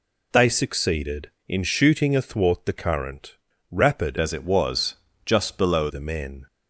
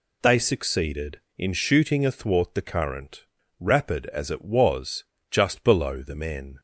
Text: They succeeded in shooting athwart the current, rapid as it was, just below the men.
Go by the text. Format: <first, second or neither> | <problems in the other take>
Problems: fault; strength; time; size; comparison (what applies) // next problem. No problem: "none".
second | changes voice from "as" to "below"; from 4.1 to 5.8 s; 1.7 s long